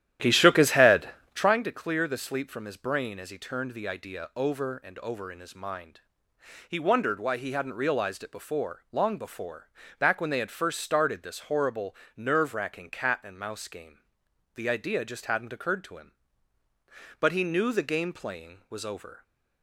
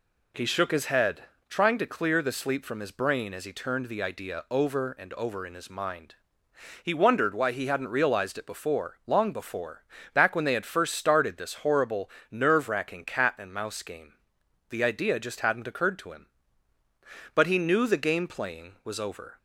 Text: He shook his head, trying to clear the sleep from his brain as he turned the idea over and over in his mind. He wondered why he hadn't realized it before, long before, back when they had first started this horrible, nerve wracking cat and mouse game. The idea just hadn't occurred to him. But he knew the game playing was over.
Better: second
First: starts louder than the rest; strong; until 1.6 s; 12 dB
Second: none

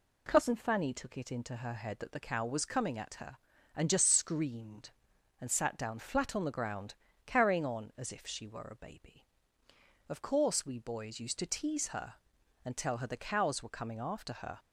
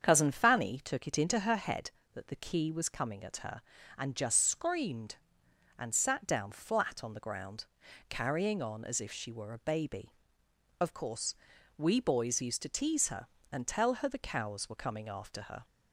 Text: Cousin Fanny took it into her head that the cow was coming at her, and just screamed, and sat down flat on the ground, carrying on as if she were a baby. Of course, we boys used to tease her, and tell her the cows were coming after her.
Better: first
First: none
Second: starts louder than the rest; strong; until 1.0 s; 7.5 dB // says "key" for "cow"; at 2.3 s

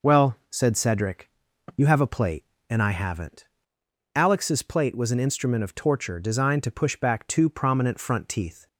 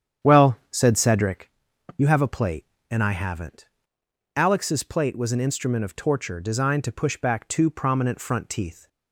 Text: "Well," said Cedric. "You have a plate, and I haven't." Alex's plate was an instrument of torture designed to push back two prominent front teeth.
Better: first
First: none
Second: starts louder than the rest; strong; until 1.5 s; 9 dB

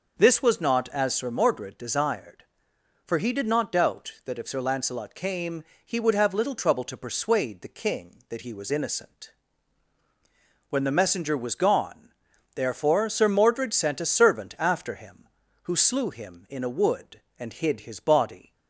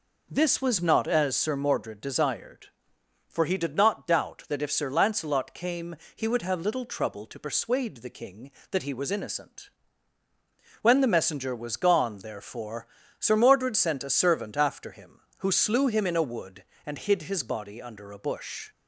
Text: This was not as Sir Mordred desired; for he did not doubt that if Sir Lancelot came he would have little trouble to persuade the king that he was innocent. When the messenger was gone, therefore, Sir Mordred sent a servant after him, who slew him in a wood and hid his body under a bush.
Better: second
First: pauses between "came" and "he"; slight; at 5.6 s; 0.22 s long // stops before "under a bush"; at 18.5 s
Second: pauses between "came" and "he"; slight; at 5.9 s; 0.18 s long

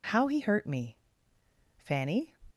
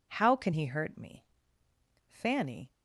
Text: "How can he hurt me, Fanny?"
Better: second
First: skips "can"; at 0.2 s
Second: none

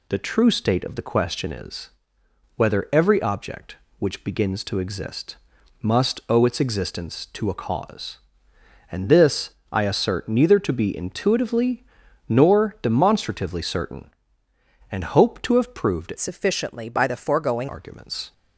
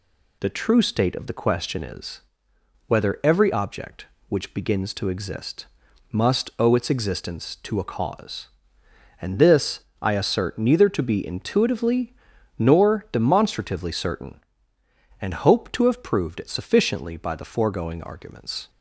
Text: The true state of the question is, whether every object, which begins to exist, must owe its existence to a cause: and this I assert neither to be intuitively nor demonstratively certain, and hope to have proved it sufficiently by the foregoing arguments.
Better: second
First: pauses between "this" and "I"; slight; at 9.5 s; 0.20 s long // pauses between "intuitively" and "nor"; at 11.8 s; 0.42 s long // changes voice from "sufficiently" to "foregoing"; from 16.1 to 17.6 s; 1.5 s long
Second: pauses between "this" and "I"; slight; at 9.8 s; 0.20 s long // pauses between "intuitively" and "nor"; at 12.1 s; 0.42 s long

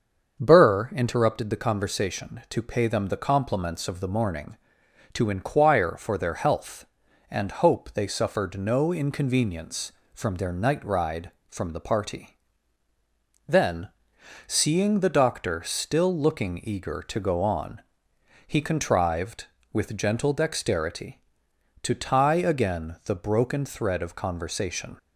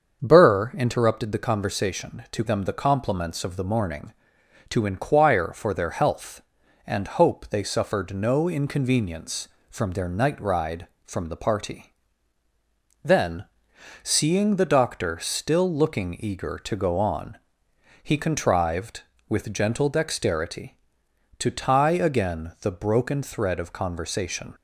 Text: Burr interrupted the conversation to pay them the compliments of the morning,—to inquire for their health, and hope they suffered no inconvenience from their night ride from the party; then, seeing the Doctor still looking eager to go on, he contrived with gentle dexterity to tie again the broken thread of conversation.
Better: first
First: starts louder than the rest; until 1.4 s; 6.5 dB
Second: starts louder than the rest; until 1.2 s; 7 dB // skips "pay"; at 2.4 s

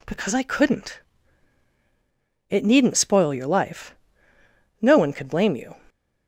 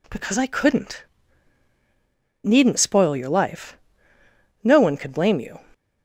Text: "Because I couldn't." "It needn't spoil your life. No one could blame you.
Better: first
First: none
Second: skips "It"; at 1.7 s

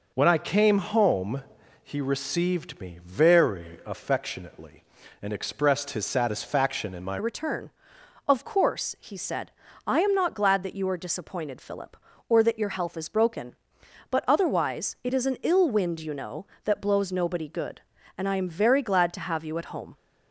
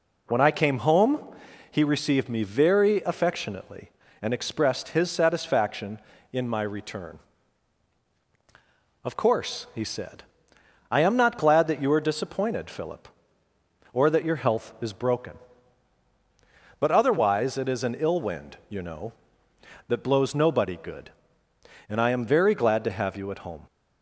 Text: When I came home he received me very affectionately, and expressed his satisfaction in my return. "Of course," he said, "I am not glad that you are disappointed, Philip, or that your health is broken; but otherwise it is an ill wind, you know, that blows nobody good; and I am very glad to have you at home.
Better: second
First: pauses between "home" and "he"; at 1.4 s; 0.42 s long // changes voice at "return"; from 7.1 s on; 12.8 s long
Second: pauses between "home" and "he"; noticeable; at 1.2 s; 0.48 s long

